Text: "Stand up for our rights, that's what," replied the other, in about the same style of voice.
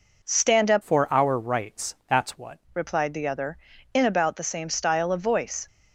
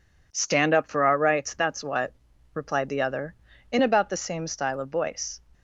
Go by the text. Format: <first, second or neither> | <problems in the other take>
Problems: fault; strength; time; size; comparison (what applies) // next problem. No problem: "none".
second | changes voice from "for" to "what"; from 0.8 to 2.5 s; 1.7 s long